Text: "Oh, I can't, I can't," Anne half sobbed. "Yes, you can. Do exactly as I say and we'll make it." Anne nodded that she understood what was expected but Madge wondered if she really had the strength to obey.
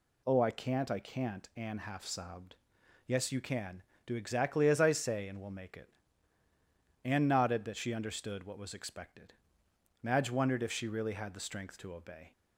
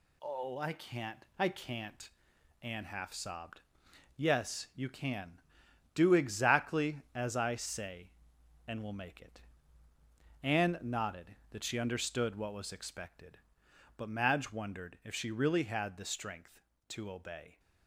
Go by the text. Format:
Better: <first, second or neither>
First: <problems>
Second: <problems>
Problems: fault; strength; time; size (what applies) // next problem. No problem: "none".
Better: second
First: skips "but"; at 9.6 s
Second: none